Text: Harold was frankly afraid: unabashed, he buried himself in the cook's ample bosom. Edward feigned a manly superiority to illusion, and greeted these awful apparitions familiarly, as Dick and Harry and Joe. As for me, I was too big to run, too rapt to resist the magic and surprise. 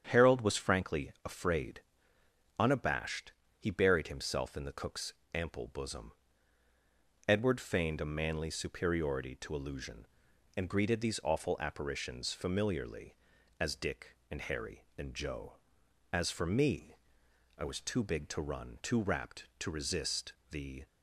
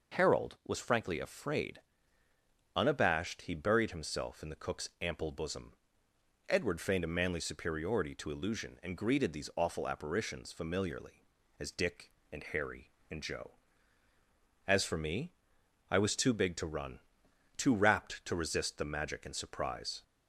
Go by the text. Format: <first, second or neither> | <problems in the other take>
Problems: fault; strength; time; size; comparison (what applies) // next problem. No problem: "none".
second | starts louder than the rest; strong; until 1.1 s; 8 dB // pauses between "cook's" and "ample"; slight; at 5.1 s; 0.20 s long // pauses between "resist" and "the"; slight; at 20.3 s; 0.18 s long // stops before "magic and surprise"; at 20.8 s